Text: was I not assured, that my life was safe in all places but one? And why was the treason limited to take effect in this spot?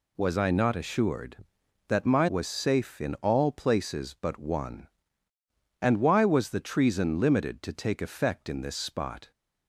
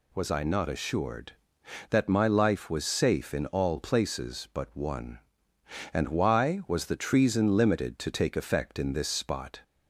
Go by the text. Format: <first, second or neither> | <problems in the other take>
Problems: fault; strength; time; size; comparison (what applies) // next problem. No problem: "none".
second | skips "life"; at 2.2 s